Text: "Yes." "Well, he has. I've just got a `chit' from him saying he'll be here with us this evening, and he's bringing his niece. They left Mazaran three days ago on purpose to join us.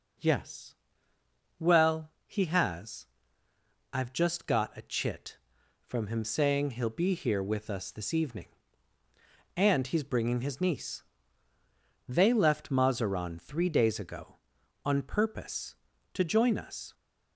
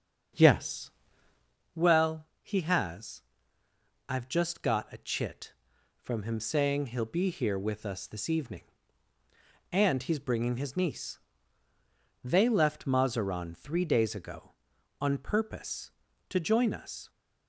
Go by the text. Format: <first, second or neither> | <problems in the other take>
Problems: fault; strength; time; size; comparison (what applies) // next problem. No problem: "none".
first | starts louder than the rest; strong; until 1.6 s; 7 dB